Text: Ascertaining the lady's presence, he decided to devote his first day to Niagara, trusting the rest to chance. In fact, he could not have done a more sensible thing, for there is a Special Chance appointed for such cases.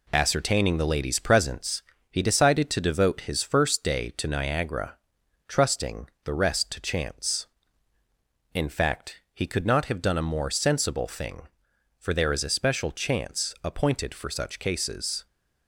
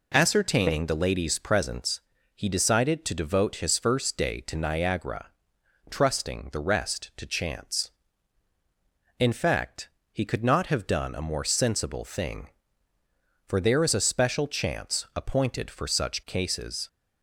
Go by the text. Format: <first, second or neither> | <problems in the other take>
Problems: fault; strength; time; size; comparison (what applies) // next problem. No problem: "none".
second | gets quieter; noticeable; throughout; 5 dB // pauses between "trusting" and "the"; slight; at 6.0 s; 0.16 s long